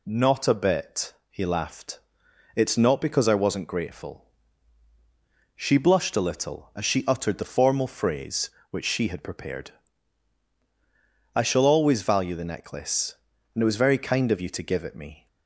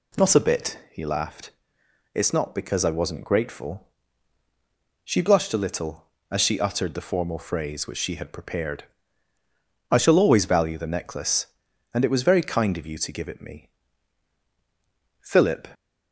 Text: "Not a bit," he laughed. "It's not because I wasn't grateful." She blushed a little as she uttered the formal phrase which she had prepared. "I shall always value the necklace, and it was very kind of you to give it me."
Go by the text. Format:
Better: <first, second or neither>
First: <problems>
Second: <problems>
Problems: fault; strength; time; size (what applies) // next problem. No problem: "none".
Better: first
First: none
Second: goes on to say "Philip"; slight; from 15.2 s on; 0.46 s long